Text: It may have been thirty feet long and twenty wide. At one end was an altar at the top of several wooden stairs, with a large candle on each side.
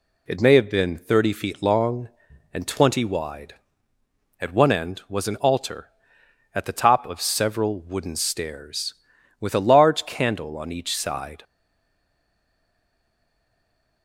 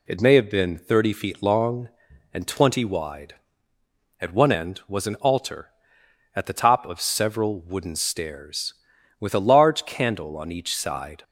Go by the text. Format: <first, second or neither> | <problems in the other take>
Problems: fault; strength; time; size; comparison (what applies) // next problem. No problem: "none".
second | stays silent after the last word; strong; from 11.4 s on; 2.6 s long